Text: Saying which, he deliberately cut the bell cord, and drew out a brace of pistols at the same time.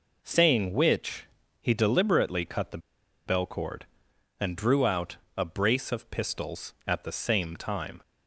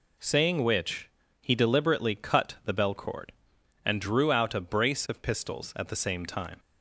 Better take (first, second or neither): second